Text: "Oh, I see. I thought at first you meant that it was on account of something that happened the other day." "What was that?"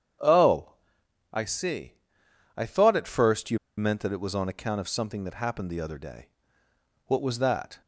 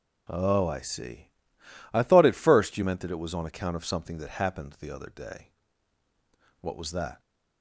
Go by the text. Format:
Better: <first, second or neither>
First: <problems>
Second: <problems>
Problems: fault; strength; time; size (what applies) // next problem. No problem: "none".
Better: second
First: starts louder than the rest; strong; until 1.8 s; 8.5 dB // pauses between "you" and "meant"; slight; at 3.5 s; 0.20 s long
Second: none